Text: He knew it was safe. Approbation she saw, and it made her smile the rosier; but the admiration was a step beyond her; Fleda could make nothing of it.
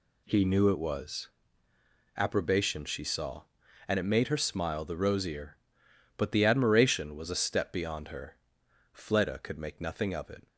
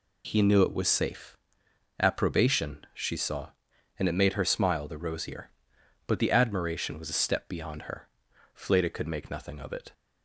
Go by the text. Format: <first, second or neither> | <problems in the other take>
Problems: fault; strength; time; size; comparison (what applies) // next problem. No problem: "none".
second | skips "safe"; at 1.7 s